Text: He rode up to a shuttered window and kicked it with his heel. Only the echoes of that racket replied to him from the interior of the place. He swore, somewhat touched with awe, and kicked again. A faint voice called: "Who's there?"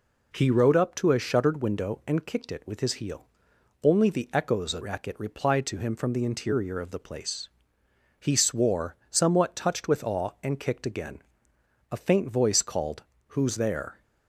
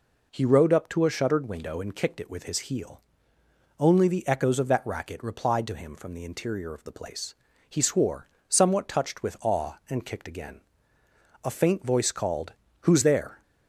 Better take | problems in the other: second | skips "that"; at 4.8 s

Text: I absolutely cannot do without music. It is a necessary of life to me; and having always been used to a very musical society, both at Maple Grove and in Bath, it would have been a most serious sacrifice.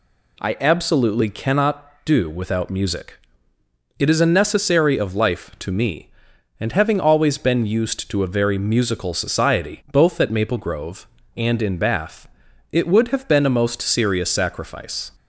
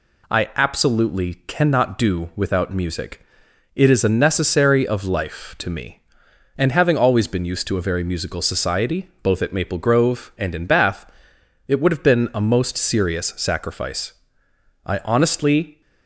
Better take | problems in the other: first | goes on to say "I honestly"; noticeable; from 14.8 s on; 0.94 s long

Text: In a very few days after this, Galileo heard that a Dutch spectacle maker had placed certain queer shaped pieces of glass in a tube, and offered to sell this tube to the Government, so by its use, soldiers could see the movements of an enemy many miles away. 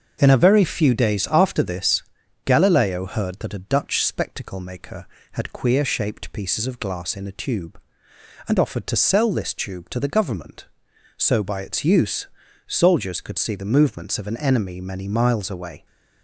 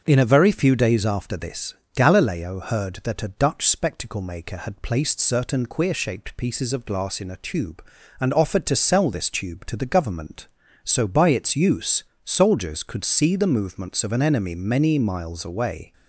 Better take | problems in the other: second | starts louder than the rest; until 1.2 s; 6.5 dB; also in the second // skips "placed certain"; at 5.5 s

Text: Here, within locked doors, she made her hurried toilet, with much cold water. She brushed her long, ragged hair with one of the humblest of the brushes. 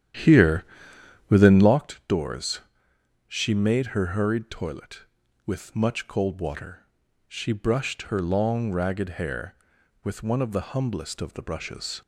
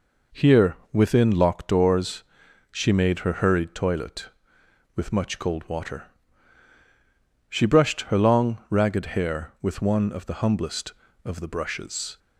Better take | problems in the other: second | starts louder than the rest; strong; until 1.8 s; 10.5 dB

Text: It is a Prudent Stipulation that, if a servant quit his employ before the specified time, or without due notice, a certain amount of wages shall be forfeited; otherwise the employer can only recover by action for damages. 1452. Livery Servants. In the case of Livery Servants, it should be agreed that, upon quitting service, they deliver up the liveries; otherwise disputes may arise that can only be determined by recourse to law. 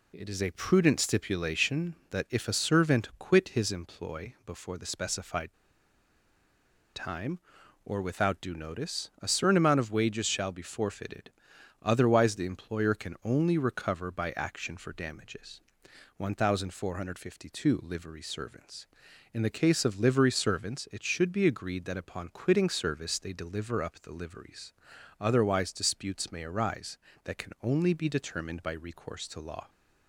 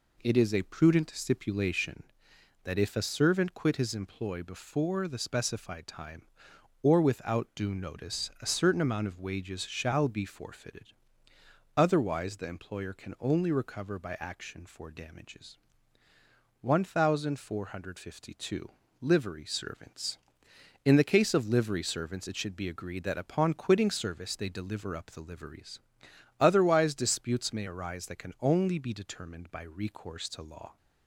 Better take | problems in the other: second | pauses between "specified" and "time"; strong; at 5.5 s; 1.4 s long

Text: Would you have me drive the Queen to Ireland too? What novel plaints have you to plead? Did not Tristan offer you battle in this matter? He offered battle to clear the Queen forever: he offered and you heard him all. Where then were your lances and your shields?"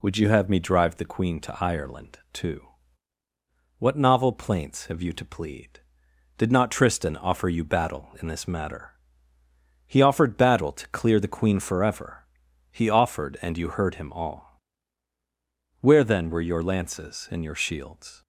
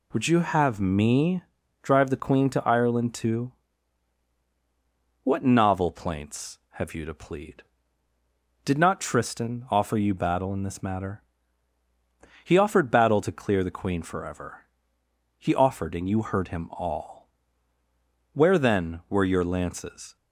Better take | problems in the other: first | pauses between "me" and "drive"; at 1.4 s; 0.40 s long // stops before "and your shields"; at 20.1 s

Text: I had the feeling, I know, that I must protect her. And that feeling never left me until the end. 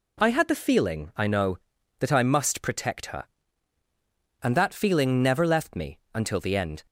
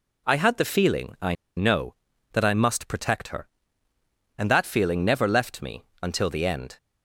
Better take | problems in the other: first | pauses between "I" and "know"; slight; at 1.3 s; 0.21 s long // pauses between "me" and "until"; slight; at 5.8 s; 0.18 s long

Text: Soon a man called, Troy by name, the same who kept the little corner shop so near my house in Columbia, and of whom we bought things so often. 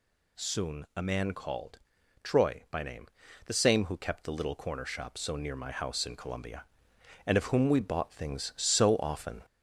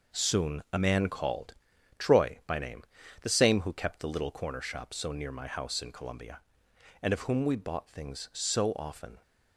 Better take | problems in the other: second | gets louder; slight; throughout; 3 dB

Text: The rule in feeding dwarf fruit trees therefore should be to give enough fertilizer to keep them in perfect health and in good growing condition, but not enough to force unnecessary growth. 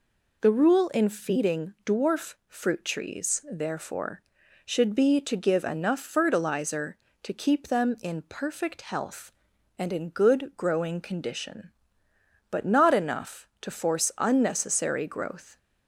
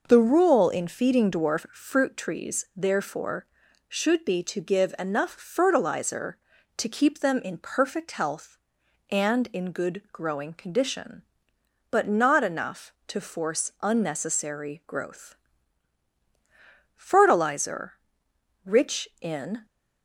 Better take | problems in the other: first | goes on to say "Fertilizer rich in"; strong; from 16.9 s on; 2.7 s long

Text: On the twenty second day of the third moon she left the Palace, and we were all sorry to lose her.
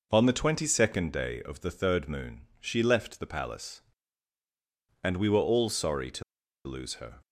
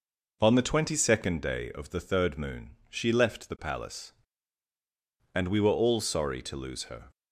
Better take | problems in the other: second | pauses between "moon" and "she"; slight; at 2.4 s; 0.18 s long; slight in the second // pauses between "to" and "lose"; at 6.2 s; 0.44 s long

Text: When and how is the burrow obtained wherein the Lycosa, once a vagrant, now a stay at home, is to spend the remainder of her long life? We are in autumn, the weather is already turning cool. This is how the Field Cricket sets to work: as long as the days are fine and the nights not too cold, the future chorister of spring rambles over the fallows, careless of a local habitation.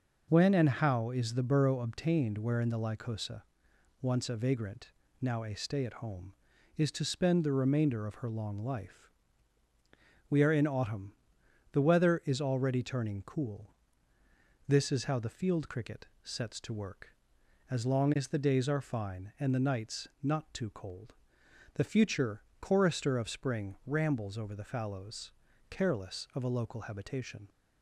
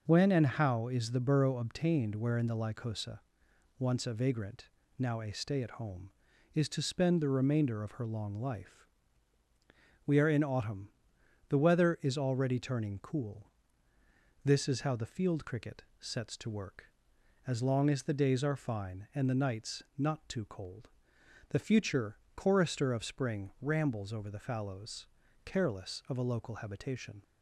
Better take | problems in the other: neither | pauses between "Cricket" and "sets"; slight; the same in both // pauses between "nights" and "not"; slight; the same in both // pauses between "future" and "chorister"; slight; the same in both

